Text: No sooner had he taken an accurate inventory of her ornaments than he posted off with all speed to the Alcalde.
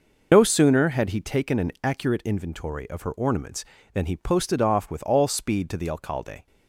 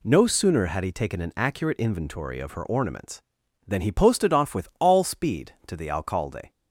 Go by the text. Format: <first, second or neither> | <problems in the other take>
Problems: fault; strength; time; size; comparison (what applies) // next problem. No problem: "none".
second | loses the start of "No"; at 0.3 s; 80 ms